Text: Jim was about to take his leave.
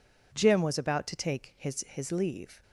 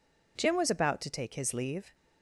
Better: second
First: says "his" twice; at 1.8 s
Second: none

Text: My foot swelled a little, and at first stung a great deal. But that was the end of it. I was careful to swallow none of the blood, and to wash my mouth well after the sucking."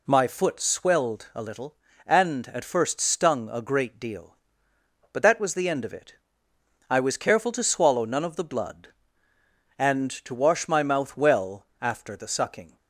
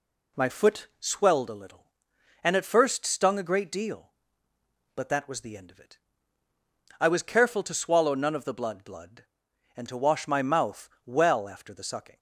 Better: first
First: none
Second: says "blood" twice; at 8.8 s // pauses between "mouth" and "well"; slight; at 10.8 s; 0.18 s long

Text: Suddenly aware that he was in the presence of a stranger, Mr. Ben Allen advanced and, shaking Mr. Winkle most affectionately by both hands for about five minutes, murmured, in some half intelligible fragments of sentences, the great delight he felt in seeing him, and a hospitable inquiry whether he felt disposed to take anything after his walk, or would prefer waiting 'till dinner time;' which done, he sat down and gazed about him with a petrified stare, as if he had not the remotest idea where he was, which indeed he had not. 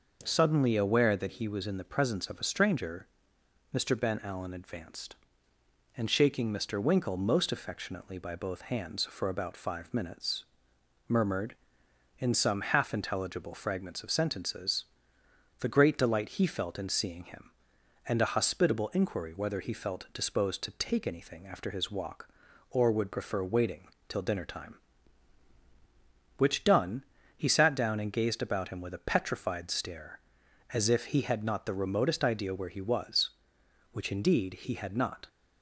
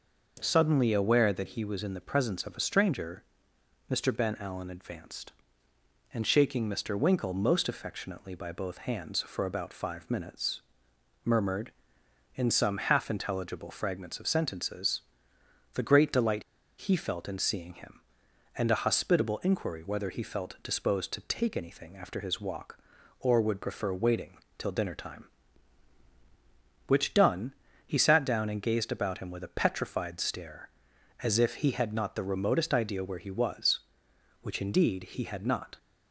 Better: first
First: pauses between "waiting" and "till"; slight; at 23.8 s; 0.20 s long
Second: pauses between "delight" and "he"; at 16.4 s; 0.36 s long // pauses between "waiting" and "till"; slight; at 24.3 s; 0.20 s long

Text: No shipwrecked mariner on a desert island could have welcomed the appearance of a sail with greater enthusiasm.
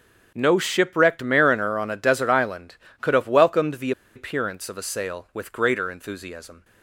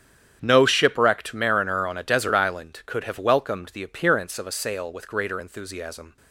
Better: second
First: starts louder than the rest; strong; until 1.3 s; 8 dB // pauses between "the" and "appearance"; slight; at 3.9 s; 0.24 s long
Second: starts louder than the rest; strong; until 1.4 s; 9 dB

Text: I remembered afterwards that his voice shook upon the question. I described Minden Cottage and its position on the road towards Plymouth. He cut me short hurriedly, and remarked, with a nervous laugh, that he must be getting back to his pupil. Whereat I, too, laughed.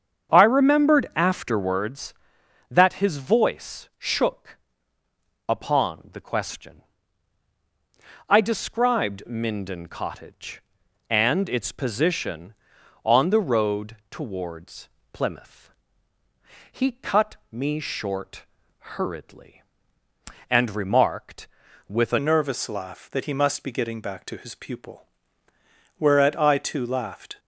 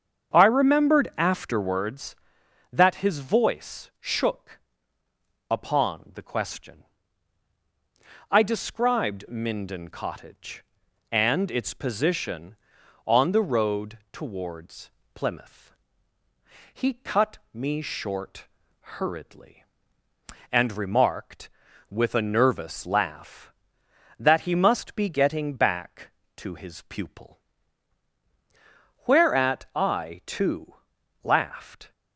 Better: second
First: starts louder than the rest; strong; until 1.4 s; 7.5 dB // pauses between "shook" and "upon"; noticeable; at 4.5 s; 0.90 s long // pauses between "towards" and "Plymouth"; slight; at 14.8 s; 0.22 s long // pauses between "cut" and "me"; slight; at 17.3 s; 0.16 s long // pauses between "short" and "hurriedly"; noticeable; at 18.4 s; 0.50 s long // changes voice at "nervous"; from 22.1 s on; 5.2 s long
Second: starts louder than the rest; strong; until 1.4 s; 7.5 dB // pauses between "shook" and "upon"; noticeable; at 4.6 s; 0.90 s long // pauses between "towards" and "Plymouth"; slight; at 14.9 s; 0.22 s long // pauses between "cut" and "me"; slight; at 17.3 s; 0.16 s long // pauses between "short" and "hurriedly"; noticeable; at 18.4 s; 0.50 s long

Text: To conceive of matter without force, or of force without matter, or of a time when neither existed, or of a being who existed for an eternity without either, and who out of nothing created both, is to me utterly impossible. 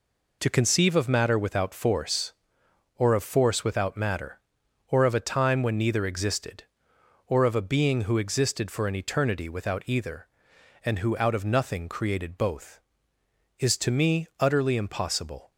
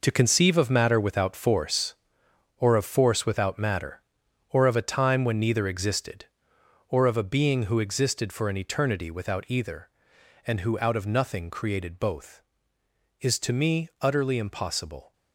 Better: first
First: none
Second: gets quieter; strong; throughout; 9.5 dB

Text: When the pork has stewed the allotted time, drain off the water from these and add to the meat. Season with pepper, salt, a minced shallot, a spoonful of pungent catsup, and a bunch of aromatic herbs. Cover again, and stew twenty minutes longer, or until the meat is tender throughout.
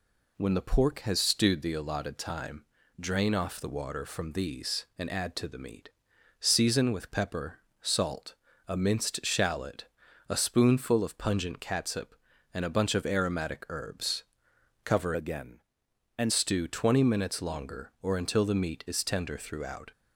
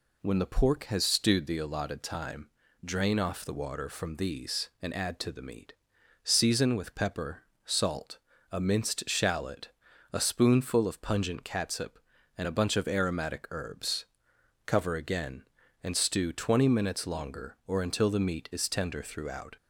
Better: second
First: changes voice from "again" to "and"; from 15.1 to 16.3 s; 1.2 s long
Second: none

